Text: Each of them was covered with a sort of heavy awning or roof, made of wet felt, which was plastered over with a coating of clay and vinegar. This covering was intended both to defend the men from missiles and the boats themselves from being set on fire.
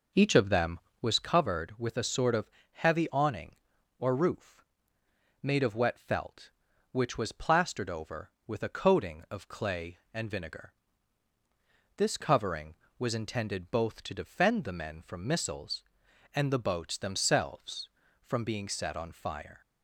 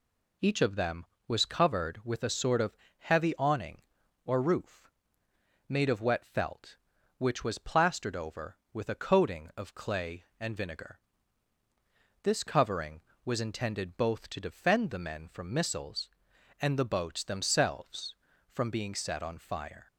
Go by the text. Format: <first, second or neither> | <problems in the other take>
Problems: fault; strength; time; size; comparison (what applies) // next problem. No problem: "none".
second | starts louder than the rest; noticeable; until 1.1 s; 5.5 dB // pauses between "of" and "heavy"; slight; at 2.4 s; 0.24 s long; slight in the second